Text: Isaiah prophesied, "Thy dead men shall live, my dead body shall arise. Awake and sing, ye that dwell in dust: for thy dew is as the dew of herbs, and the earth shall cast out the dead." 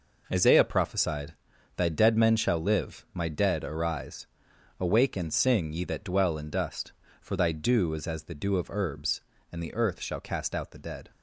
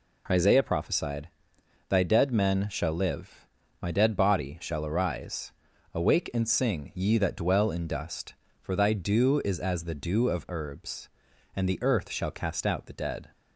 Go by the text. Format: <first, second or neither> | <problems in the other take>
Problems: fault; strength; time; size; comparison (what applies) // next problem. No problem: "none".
second | skips "body shall"; at 3.6 s